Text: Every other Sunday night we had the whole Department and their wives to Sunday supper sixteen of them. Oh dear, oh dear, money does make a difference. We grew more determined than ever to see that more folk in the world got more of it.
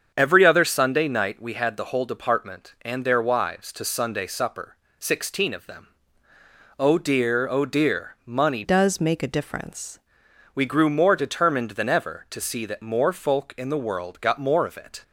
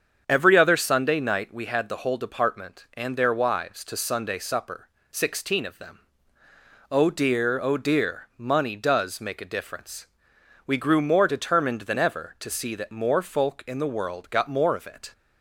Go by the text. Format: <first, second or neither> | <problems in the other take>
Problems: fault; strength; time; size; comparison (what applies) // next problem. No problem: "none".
second | starts louder than the rest; strong; until 1.1 s; 7 dB; strong in the second // pauses between "supper" and "sixteen"; slight; at 4.7 s; 0.22 s long; slight in the second // changes voice from "does" to "difference"; from 8.6 to 10.0 s; 1.4 s long